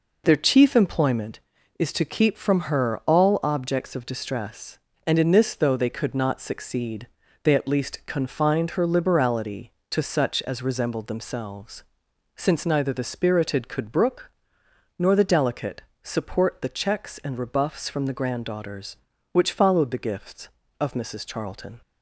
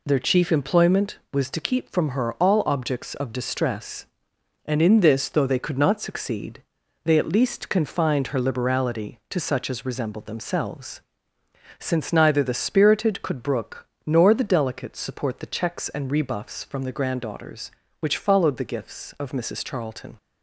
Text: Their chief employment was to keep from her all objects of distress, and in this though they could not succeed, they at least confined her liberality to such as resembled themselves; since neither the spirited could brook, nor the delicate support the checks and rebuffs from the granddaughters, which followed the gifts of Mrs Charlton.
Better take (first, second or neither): second